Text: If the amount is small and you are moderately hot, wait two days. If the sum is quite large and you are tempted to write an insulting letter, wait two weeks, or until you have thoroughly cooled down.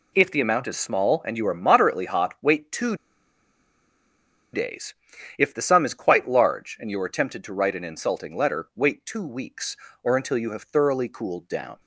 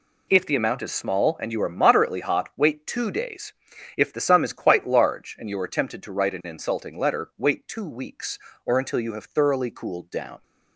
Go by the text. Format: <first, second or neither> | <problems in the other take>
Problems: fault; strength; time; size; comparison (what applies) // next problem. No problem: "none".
second | pauses between "two" and "days"; strong; at 2.9 s; 1.5 s long